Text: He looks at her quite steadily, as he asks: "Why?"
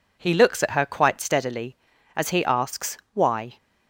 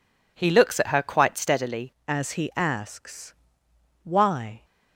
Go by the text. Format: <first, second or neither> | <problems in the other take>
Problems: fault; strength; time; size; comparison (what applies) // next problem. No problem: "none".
first | changes voice at "as"; from 2.0 s on; 2.6 s long